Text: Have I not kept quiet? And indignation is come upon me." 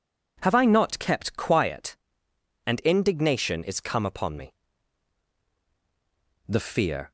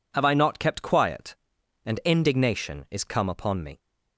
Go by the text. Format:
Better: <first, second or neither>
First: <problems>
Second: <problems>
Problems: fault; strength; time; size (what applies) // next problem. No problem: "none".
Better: second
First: goes on to say "The fear"; noticeable; from 6.4 s on; 0.64 s long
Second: none